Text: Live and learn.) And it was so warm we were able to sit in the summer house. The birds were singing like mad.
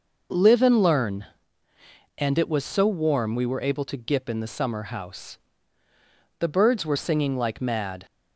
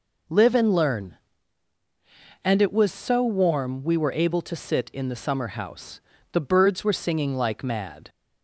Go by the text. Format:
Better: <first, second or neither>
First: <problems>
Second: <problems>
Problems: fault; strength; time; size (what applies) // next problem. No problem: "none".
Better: second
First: says "gip" for "sit"; at 3.9 s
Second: none